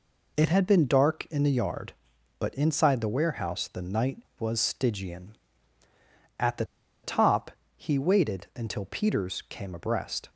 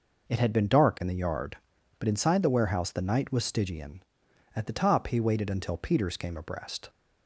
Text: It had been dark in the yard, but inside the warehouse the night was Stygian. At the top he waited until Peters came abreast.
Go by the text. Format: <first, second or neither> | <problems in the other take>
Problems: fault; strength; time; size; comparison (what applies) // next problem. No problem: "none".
second | pauses between "the" and "top"; at 6.6 s; 0.38 s long // pauses between "top" and "he"; slight; at 7.4 s; 0.26 s long